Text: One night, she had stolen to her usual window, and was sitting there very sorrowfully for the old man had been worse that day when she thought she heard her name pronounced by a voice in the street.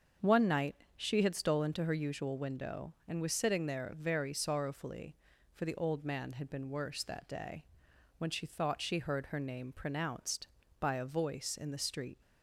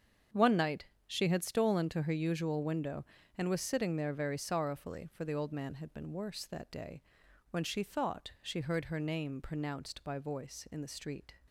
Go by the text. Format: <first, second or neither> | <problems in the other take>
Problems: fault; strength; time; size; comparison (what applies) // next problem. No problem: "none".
first | starts louder than the rest; strong; until 1.5 s; 7.5 dB; also in the first // pauses between "day" and "when"; noticeable; at 7.0 s; 0.48 s long; noticeable in the first // skips "a"; at 10.1 s